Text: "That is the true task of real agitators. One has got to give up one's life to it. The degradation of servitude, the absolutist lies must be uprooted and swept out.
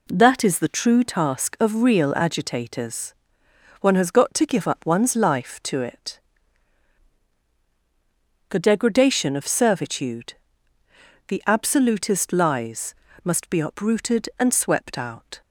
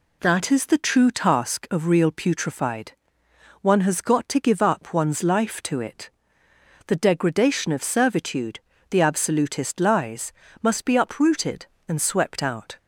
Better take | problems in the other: first | says "putrefied" for "agitators"; at 2.0 s // pauses between "lies" and "must"; slight; at 10.3 s; 0.28 s long; slight in the first

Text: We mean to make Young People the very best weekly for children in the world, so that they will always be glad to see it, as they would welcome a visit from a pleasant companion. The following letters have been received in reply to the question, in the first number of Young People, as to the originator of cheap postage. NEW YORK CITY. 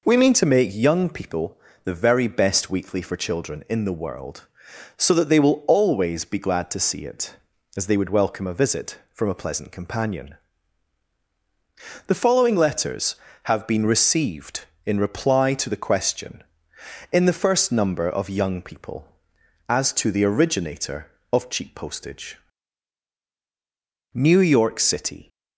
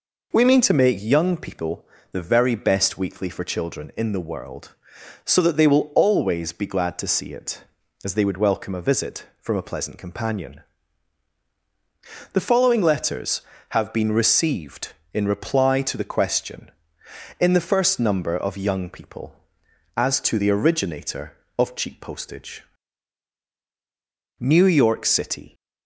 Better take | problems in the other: neither | pauses between "People" and "the"; slight; the same in both

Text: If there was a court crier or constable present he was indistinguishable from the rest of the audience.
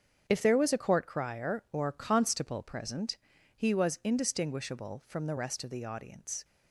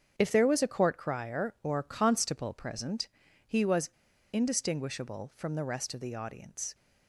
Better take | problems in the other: first | starts louder than the rest; strong; until 1.1 s; 7.5 dB; strong in the first // pauses between "present" and "he"; at 3.0 s; 0.42 s long; also in the first // pauses between "was" and "indistinguishable"; at 3.9 s; 0.41 s long

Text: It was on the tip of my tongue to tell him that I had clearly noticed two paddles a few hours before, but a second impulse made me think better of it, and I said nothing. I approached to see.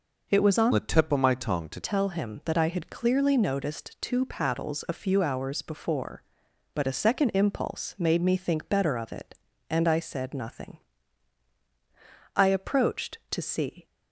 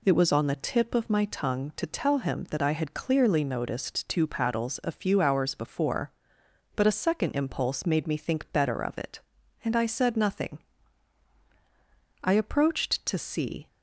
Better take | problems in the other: second | changes voice from "the" to "to"; from 0.7 to 1.7 s; 1.0 s long

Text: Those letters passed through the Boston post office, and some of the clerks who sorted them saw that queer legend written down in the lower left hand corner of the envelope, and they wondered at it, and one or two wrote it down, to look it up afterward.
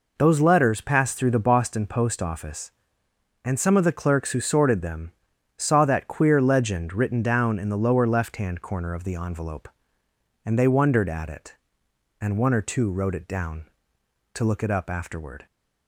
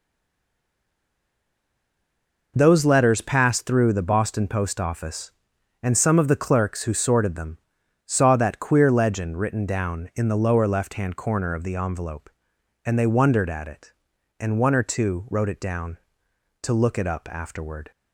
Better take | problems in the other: first | stays silent before the first word; strong; until 2.5 s; 2.5 s long // pauses between "them" and "saw"; noticeable; at 7.5 s; 0.48 s long; noticeable in the first

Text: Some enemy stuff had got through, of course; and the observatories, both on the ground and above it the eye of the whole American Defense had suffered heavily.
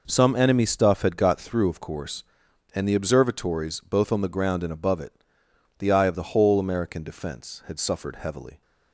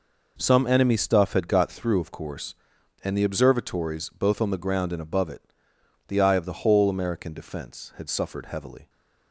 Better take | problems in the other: neither | pauses between "it" and "the"; noticeable; the same in both

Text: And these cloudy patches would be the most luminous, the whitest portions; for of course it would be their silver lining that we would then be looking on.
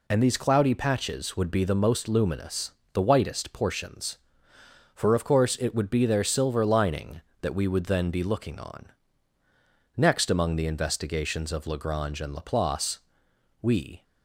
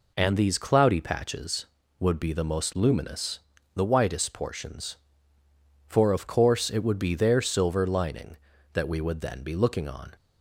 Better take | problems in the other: second | goes on to say "Next among the investigations of Lagrange and Laplace we"; strong; from 9.9 s on; 4.0 s long

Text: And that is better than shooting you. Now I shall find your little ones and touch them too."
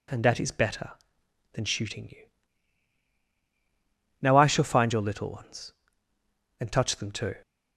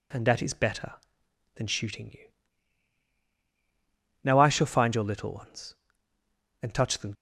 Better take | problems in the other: first | stops before "too"; at 7.1 s

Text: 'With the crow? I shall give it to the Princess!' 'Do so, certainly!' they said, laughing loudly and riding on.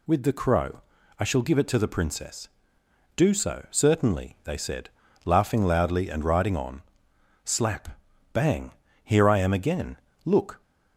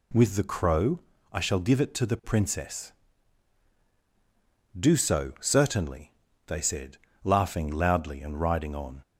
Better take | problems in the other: second | goes on to say "Slap bang here I am again Look"; strong; from 7.4 s on; 3.1 s long

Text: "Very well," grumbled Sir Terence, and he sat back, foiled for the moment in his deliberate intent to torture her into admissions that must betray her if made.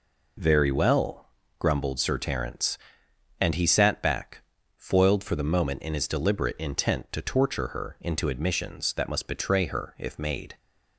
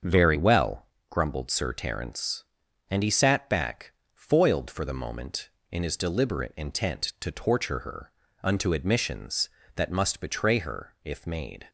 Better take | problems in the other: first | starts louder than the rest; until 1.2 s; 6.5 dB // says "unto" for "into"; at 8.4 s

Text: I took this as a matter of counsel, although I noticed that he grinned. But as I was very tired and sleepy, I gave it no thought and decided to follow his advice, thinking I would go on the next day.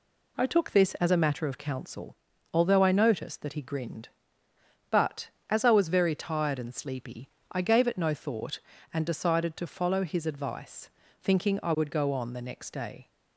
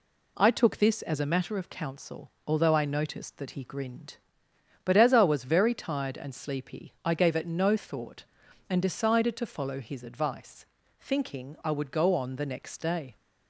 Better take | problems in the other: neither | none

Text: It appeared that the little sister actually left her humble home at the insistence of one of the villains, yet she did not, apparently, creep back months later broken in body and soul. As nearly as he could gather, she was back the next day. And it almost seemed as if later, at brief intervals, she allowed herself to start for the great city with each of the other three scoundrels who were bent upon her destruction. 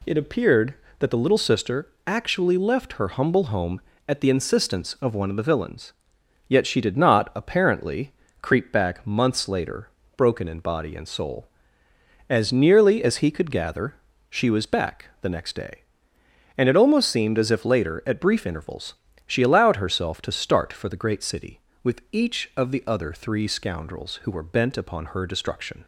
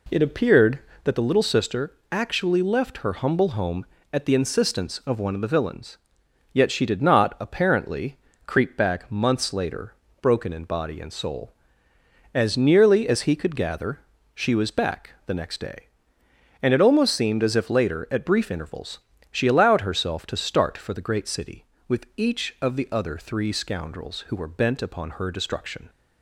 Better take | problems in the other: first | starts louder than the rest; slight; until 1.1 s; 2.5 dB // pauses between "sister" and "actually"; slight; at 1.9 s; 0.18 s long; slight in the first // pauses between "later" and "broken"; slight; at 9.9 s; 0.28 s long; slight in the first

